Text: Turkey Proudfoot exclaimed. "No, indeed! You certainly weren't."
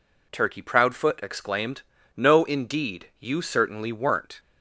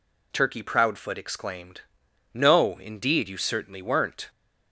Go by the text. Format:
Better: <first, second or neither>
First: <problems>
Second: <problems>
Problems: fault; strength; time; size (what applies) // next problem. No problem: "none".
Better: neither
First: none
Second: none